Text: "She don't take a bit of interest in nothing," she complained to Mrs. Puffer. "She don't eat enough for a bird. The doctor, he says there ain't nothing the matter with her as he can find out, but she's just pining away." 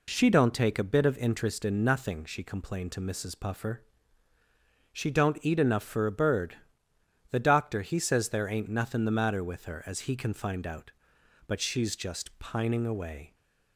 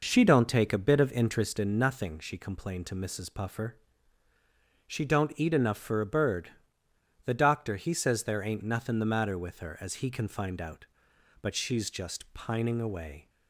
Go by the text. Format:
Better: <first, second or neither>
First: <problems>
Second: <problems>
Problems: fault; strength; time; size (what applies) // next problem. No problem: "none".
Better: first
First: none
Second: starts louder than the rest; noticeable; until 1.7 s; 5.5 dB